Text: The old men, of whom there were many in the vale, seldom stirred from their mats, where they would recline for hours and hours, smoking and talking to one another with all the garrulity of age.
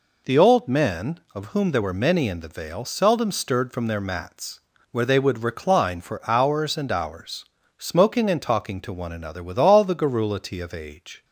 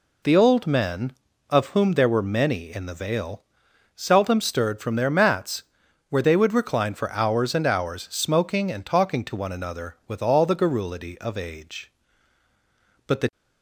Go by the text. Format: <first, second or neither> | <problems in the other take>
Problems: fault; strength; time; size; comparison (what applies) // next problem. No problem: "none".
first | goes on to say "But the"; slight; from 13.0 s on; 0.24 s long